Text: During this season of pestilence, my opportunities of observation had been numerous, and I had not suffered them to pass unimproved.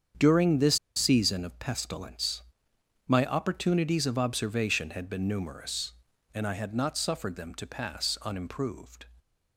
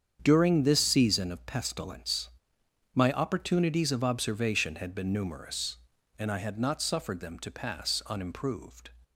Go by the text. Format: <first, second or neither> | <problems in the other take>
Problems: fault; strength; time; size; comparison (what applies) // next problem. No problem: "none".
second | starts louder than the rest; strong; until 1.3 s; 7.5 dB; strong in the second // pauses between "this" and "season"; slight; at 0.7 s; 0.20 s long